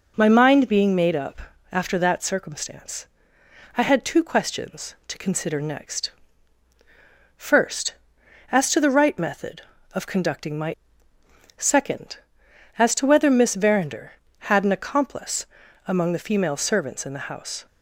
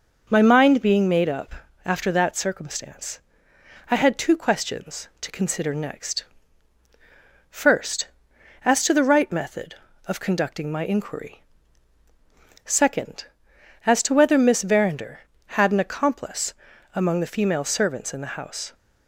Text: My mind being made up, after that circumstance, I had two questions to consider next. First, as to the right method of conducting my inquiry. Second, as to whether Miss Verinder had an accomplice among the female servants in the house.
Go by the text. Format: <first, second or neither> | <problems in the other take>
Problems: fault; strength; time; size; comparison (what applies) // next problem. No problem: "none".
second | skips "inquiry"; at 11.1 s // pauses between "accomplice" and "among"; at 15.4 s; 0.40 s long; also in the second